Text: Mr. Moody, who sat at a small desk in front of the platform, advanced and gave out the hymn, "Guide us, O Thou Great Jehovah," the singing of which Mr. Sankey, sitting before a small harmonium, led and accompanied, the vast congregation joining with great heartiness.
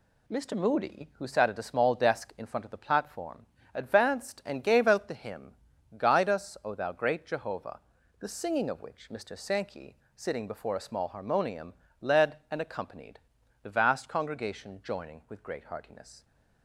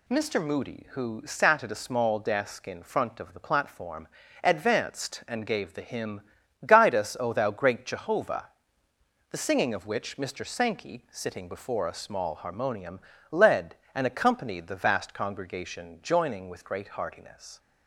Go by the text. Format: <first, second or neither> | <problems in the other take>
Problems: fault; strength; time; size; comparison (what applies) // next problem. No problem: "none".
first | skips "out"; at 5.7 s